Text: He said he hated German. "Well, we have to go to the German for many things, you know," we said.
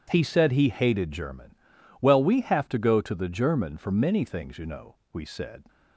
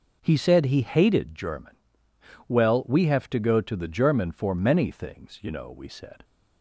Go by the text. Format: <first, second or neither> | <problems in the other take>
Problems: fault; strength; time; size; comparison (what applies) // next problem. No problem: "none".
neither | none